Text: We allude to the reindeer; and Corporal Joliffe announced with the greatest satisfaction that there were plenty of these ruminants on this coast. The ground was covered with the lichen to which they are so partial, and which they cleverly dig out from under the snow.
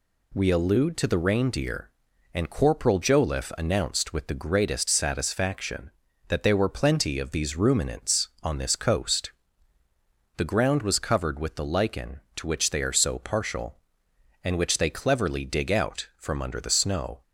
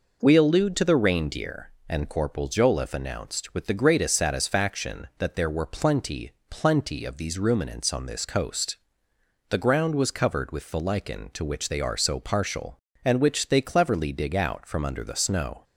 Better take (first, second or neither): first